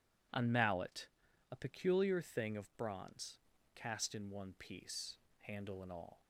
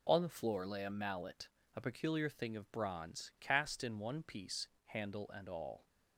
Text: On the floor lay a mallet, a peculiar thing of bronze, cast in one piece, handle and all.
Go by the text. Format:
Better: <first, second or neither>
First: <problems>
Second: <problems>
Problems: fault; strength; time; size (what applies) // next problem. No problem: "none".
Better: second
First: skips "the floor lay a"; at 0.5 s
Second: none